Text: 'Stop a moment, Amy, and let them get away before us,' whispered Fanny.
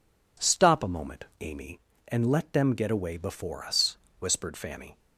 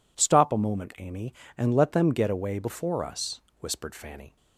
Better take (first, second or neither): neither